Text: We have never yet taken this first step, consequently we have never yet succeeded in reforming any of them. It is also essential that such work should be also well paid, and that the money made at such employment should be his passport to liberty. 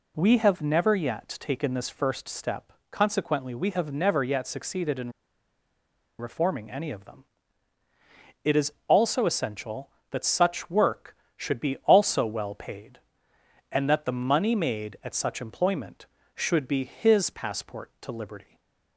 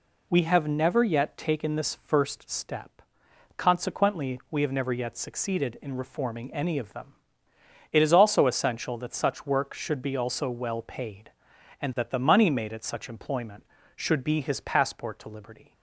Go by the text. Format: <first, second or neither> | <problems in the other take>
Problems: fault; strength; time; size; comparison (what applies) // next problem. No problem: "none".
second | pauses between "in" and "reforming"; at 5.1 s; 1.0 s long // pauses between "is" and "also"; slight; at 8.7 s; 0.16 s long // stays silent after the last word; slight; from 18.4 s on; 0.5 s long